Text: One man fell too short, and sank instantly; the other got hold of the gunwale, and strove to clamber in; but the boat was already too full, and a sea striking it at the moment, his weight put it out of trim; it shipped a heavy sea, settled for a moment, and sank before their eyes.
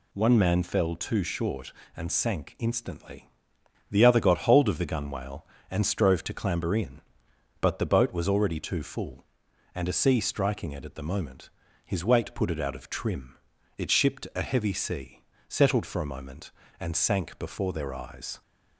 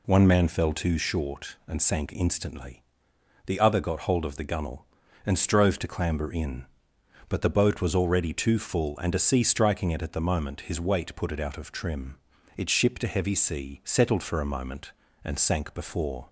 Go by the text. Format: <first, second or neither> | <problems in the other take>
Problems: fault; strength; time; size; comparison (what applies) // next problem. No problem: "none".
first | stops before "their eyes"; at 16.2 s